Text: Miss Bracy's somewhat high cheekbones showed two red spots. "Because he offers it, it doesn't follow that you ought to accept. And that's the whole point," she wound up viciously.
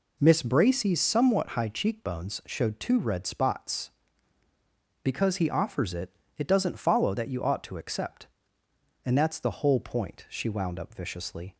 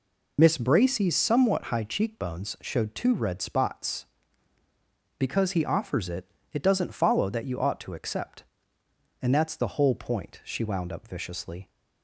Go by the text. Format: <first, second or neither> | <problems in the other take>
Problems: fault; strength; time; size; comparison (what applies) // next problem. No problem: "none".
first | loses the start of "Miss"; at 0.3 s; 40 ms